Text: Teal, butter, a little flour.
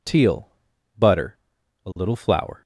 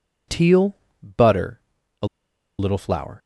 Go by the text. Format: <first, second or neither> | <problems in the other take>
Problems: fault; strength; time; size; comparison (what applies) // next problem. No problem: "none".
first | pauses between "a" and "little"; noticeable; at 2.0 s; 0.51 s long